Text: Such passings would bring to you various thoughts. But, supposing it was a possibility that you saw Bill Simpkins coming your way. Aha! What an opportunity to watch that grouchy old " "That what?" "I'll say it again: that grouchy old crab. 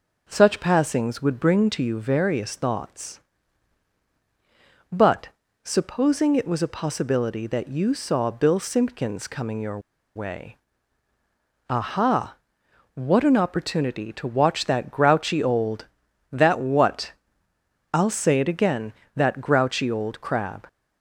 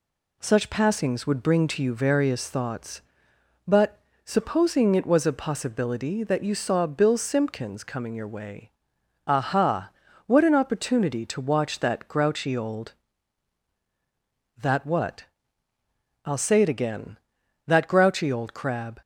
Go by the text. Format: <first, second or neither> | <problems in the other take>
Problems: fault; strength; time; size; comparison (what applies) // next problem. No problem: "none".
second | pauses between "your" and "way"; slight; at 9.7 s; 0.35 s long